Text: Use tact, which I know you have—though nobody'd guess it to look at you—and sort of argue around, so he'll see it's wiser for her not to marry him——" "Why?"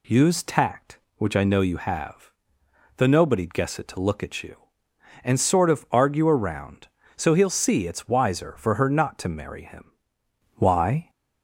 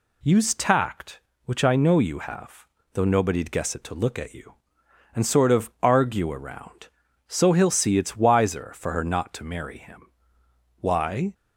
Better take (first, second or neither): neither